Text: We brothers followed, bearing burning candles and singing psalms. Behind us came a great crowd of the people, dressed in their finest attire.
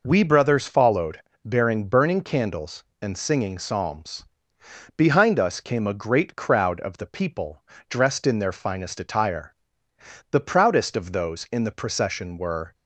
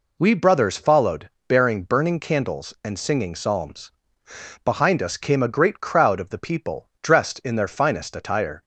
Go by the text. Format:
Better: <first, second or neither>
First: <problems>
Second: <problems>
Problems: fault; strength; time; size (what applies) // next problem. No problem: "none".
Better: second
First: goes on to say "The proudest of those in the procession were"; strong; from 10.3 s on; 2.4 s long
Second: none